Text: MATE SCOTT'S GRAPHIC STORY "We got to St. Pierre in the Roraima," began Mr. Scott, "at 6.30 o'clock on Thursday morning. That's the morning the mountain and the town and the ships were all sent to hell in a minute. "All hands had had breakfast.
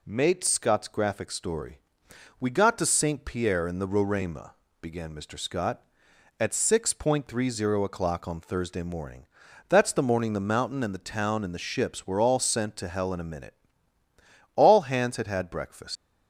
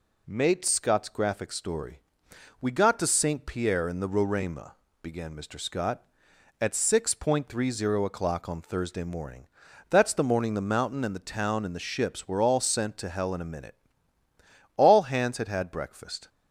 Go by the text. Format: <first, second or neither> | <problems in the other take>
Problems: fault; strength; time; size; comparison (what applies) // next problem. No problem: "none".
second | pauses between "STORY" and "We"; noticeable; at 1.7 s; 0.60 s long; noticeable in the second // leaves "breakfast" unfinished; at 15.9 s; 120 ms